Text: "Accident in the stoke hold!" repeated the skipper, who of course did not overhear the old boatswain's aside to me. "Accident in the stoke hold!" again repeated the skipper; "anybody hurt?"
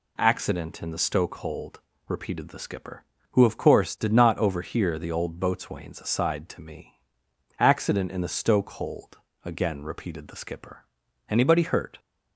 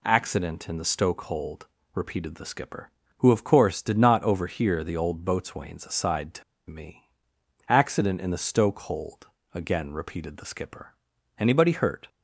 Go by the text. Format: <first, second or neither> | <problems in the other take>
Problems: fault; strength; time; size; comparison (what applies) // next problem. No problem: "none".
first | pauses between "to" and "me"; slight; at 6.4 s; 0.27 s long